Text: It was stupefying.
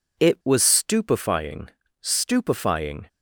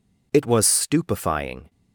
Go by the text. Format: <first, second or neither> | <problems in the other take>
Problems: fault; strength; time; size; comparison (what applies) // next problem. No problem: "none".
second | says "stupefying" twice; at 1.9 s